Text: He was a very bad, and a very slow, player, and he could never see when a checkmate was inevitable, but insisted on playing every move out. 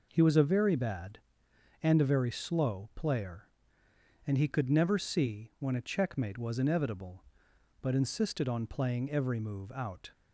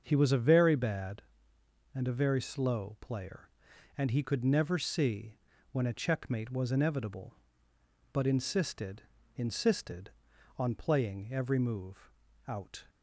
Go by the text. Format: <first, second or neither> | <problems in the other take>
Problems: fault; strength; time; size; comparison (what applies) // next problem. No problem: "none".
first | starts louder than the rest; until 1.0 s; 6.5 dB // pauses between "see" and "when"; slight; at 5.3 s; 0.36 s long // says "insisted" twice; at 9.3 s // pauses between "move" and "out"; slight; at 12.1 s; 0.36 s long